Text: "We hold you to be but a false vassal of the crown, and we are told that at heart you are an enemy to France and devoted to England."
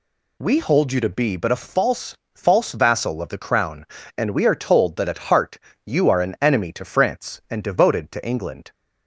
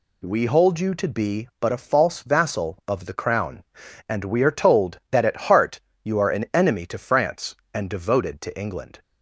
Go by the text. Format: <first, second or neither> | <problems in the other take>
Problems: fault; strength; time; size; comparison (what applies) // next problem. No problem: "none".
second | says "false" twice; at 2.3 s // pauses between "heart" and "you"; slight; at 5.5 s; 0.26 s long; slight in the second